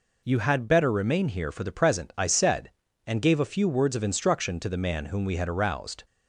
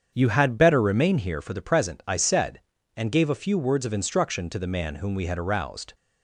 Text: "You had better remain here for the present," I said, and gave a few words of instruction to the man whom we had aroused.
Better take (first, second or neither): first